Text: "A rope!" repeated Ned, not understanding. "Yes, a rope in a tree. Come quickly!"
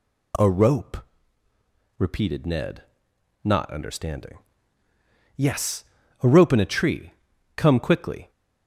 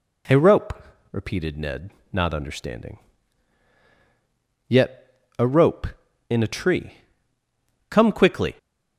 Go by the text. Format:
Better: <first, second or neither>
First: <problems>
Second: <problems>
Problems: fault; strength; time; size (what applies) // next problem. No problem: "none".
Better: first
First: none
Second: says "Yet" for "Yes"; at 4.6 s